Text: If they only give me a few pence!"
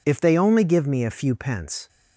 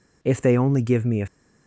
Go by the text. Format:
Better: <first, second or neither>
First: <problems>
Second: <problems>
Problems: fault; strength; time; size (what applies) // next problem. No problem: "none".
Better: first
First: none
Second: stops before "few pence"; at 1.2 s